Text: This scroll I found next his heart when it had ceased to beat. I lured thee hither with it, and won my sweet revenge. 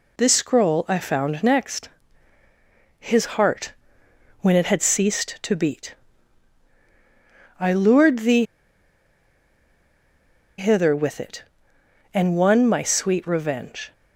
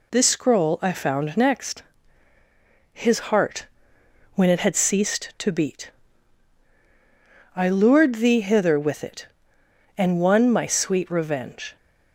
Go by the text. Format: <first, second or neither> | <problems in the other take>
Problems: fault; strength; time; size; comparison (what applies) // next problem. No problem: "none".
second | pauses between "next" and "his"; at 1.8 s; 1.1 s long; also in the second // pauses between "heart" and "when"; noticeable; at 3.7 s; 0.68 s long; noticeable in the second // pauses between "thee" and "hither"; strong; at 8.4 s; 2.1 s long